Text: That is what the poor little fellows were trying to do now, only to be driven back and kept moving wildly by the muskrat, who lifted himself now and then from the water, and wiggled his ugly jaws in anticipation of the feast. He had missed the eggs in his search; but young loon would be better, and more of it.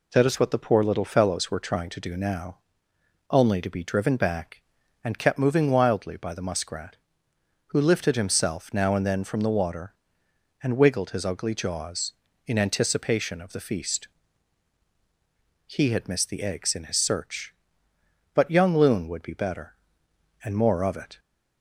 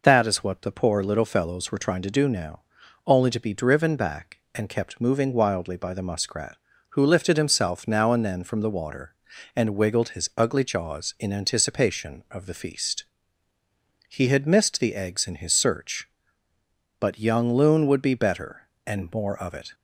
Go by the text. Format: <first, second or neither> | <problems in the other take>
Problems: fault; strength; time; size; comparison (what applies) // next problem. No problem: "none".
neither | none